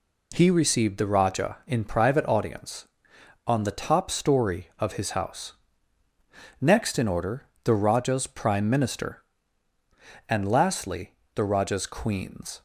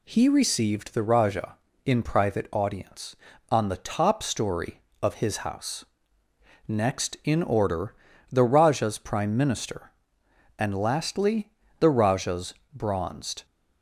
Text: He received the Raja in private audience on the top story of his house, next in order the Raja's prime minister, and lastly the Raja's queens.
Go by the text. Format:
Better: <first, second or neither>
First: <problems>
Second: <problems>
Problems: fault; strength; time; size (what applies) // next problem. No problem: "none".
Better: first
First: pauses between "order" and "the"; slight; at 7.4 s; 0.20 s long // pauses between "lastly" and "the"; slight; at 11.1 s; 0.22 s long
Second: pauses between "order" and "the"; slight; at 7.9 s; 0.36 s long // pauses between "lastly" and "the"; slight; at 11.4 s; 0.30 s long // says "bronzed" for "queens"; at 12.7 s